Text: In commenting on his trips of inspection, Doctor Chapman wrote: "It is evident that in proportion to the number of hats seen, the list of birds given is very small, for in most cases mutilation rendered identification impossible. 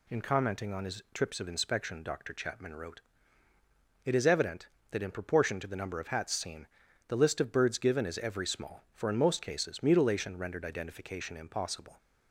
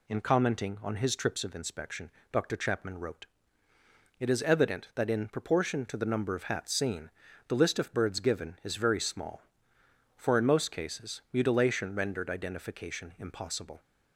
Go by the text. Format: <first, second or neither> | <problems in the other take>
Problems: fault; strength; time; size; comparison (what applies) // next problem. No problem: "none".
second | says "every" for "very"; at 8.1 s